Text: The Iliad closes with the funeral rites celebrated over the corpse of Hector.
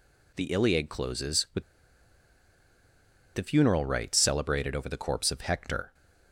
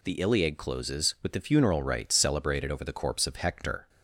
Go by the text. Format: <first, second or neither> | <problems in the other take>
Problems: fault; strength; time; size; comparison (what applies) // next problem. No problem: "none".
second | pauses between "with" and "the"; strong; at 1.6 s; 1.7 s long